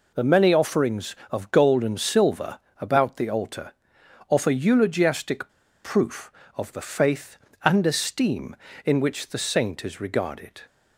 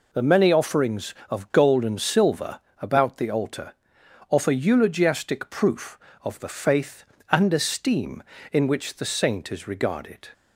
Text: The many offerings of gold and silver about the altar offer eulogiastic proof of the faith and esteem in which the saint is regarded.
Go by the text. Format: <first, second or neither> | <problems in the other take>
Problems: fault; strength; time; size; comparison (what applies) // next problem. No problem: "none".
second | pauses between "silver" and "about"; slight; at 2.5 s; 0.20 s long; slight in the second // pauses between "altar" and "offer"; noticeable; at 3.7 s; 0.56 s long; noticeable in the second // pauses between "eulogiastic" and "proof"; slight; at 5.4 s; 0.34 s long